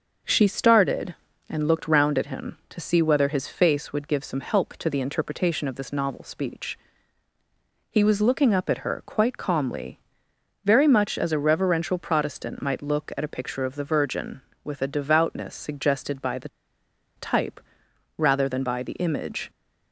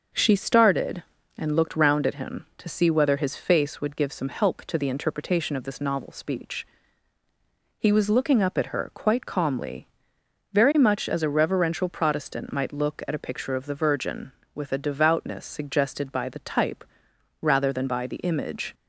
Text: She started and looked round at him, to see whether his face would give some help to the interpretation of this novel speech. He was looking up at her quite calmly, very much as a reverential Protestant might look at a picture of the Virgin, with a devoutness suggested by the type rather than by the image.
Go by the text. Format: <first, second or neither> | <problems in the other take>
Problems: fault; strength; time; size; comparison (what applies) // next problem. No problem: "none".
second | starts louder than the rest; noticeable; until 1.5 s; 6 dB; noticeable in the second // pauses between "the" and "type"; noticeable; at 16.4 s; 0.67 s long // pauses between "type" and "rather"; noticeable; at 17.6 s; 0.56 s long; noticeable in the second